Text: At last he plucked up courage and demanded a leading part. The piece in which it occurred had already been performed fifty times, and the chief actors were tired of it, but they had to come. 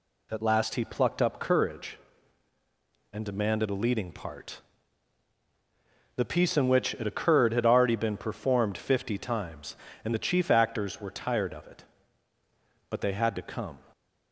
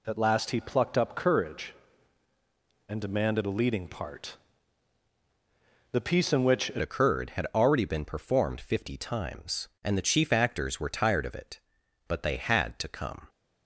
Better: first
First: none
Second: changes voice at "occurred"; from 6.8 s on; 6.4 s long

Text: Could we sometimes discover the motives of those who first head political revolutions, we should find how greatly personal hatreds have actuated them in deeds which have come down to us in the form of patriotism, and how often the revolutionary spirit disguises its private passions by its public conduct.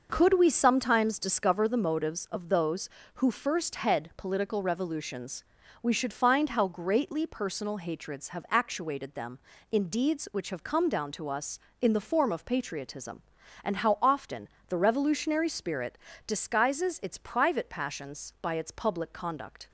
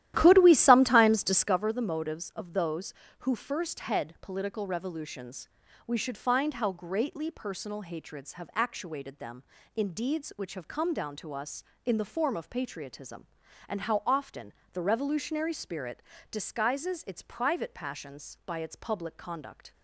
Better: first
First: pauses between "often" and "the"; slight; at 14.4 s; 0.18 s long // pauses between "spirit" and "disguises"; slight; at 15.9 s; 0.30 s long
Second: starts louder than the rest; strong; until 1.6 s; 13 dB // pauses between "often" and "the"; slight; at 14.5 s; 0.18 s long // pauses between "spirit" and "disguises"; slight; at 16.0 s; 0.30 s long

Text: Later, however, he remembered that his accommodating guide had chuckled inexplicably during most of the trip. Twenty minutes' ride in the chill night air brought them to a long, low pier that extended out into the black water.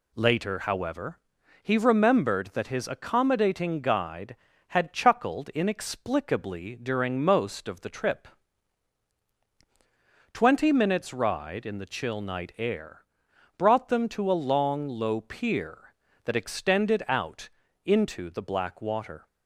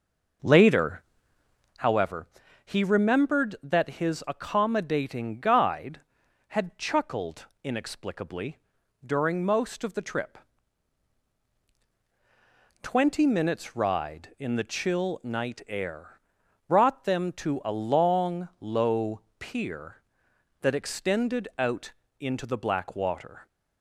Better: first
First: pauses between "air" and "brought"; noticeable; at 13.0 s; 0.52 s long // pauses between "out" and "into"; slight; at 17.4 s; 0.36 s long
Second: starts louder than the rest; noticeable; until 1.8 s; 6 dB // pauses between "chuckled" and "inexplicably"; slight; at 7.4 s; 0.18 s long // pauses between "inexplicably" and "during"; noticeable; at 8.5 s; 0.48 s long // pauses between "air" and "brought"; noticeable; at 16.1 s; 0.48 s long // pauses between "low" and "pier"; slight; at 19.1 s; 0.20 s long // pauses between "out" and "into"; slight; at 21.9 s; 0.28 s long

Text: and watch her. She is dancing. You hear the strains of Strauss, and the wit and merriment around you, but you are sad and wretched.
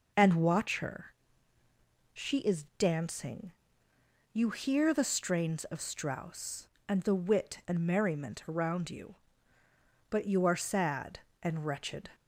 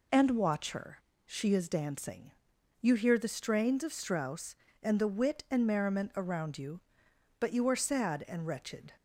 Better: neither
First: none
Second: none

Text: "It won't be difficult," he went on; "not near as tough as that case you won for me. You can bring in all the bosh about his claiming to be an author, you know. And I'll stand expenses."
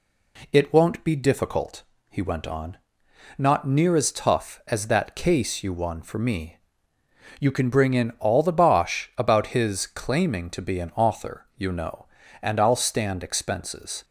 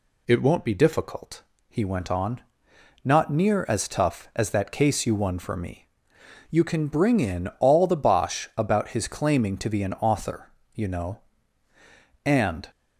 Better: first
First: none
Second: stops before "I'll stand expenses"; at 12.7 s

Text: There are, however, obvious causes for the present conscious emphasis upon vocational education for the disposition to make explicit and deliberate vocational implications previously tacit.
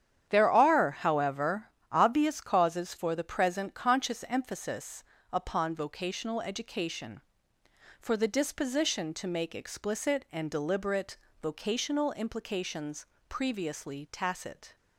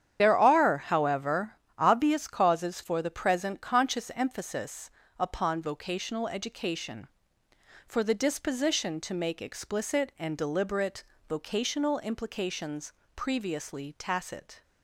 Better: first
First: starts louder than the rest; strong; until 1.3 s; 9.5 dB // pauses between "emphasis" and "upon"; slight; at 5.0 s; 0.30 s long // pauses between "deliberate" and "vocational"; slight; at 11.1 s; 0.26 s long // pauses between "implications" and "previously"; slight; at 13.0 s; 0.22 s long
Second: loses the start of "There"; at 0.1 s; 40 ms // starts louder than the rest; strong; until 1.2 s; 9.5 dB // pauses between "emphasis" and "upon"; slight; at 4.8 s; 0.30 s long // pauses between "deliberate" and "vocational"; slight; at 11.0 s; 0.26 s long // pauses between "implications" and "previously"; slight; at 12.9 s; 0.22 s long

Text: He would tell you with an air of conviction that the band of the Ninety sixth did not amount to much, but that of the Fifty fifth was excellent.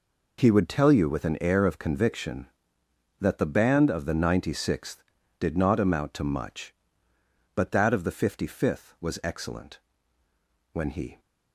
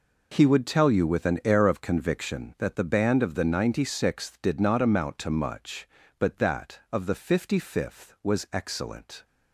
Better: second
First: goes on to say "When he"; slight; from 10.7 s on; 0.48 s long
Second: none

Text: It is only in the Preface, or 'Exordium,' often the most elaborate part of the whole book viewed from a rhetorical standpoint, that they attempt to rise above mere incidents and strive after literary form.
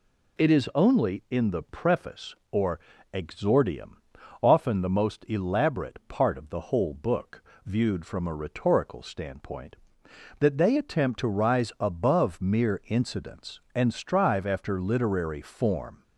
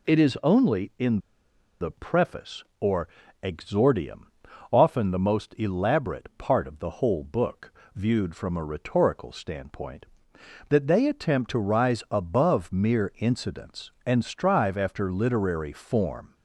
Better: first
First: pauses between "or" and "Exordium"; slight; at 2.7 s; 0.34 s long // pauses between "book" and "viewed"; slight; at 7.4 s; 0.22 s long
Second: pauses between "in" and "the"; noticeable; at 1.1 s; 0.63 s long // pauses between "or" and "Exordium"; slight; at 3.0 s; 0.36 s long // pauses between "book" and "viewed"; slight; at 7.7 s; 0.22 s long

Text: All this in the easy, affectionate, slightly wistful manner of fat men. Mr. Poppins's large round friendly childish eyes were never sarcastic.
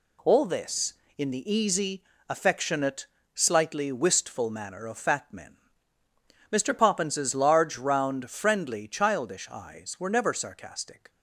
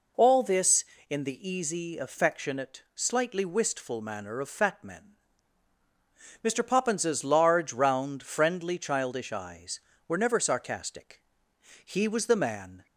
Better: first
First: none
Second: goes on to say "He was the man"; noticeable; from 11.8 s on; 0.98 s long

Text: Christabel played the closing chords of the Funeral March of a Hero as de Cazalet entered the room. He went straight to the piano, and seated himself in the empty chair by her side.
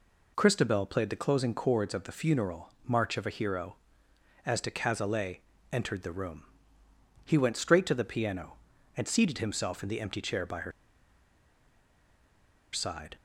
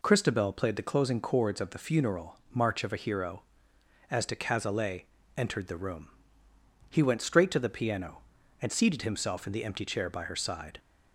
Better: second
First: pauses between "Funeral" and "March"; slight; at 2.6 s; 0.16 s long // pauses between "Cazalet" and "entered"; slight; at 5.3 s; 0.32 s long // pauses between "her" and "side"; strong; at 10.7 s; 2.0 s long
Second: pauses between "Funeral" and "March"; slight; at 2.3 s; 0.16 s long // pauses between "Cazalet" and "entered"; slight; at 5.0 s; 0.32 s long

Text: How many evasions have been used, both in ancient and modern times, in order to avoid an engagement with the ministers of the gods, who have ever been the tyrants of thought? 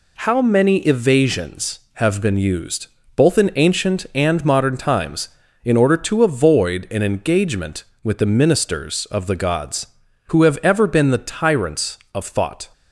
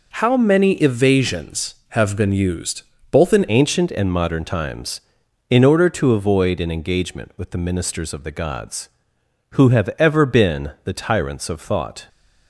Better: first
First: none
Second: changes voice at "ancient"; from 3.4 s on; 8.6 s long

